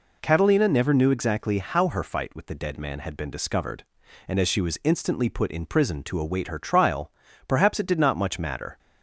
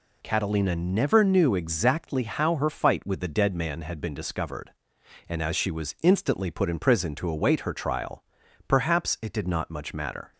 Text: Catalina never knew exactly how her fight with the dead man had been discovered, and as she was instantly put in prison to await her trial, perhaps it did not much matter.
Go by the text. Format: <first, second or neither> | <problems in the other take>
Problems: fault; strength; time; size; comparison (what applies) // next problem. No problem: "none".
neither | none